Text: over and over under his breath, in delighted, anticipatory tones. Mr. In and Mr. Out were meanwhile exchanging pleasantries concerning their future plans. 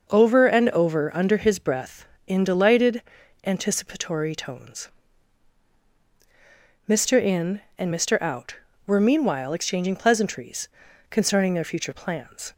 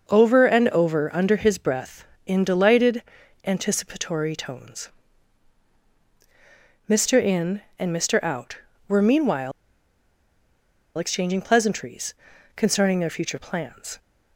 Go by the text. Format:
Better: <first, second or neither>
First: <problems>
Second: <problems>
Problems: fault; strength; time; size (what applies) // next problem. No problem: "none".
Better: first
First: pauses between "pleasantries" and "concerning"; at 10.6 s; 0.40 s long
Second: pauses between "meanwhile" and "exchanging"; strong; at 9.5 s; 1.4 s long // pauses between "pleasantries" and "concerning"; at 12.1 s; 0.40 s long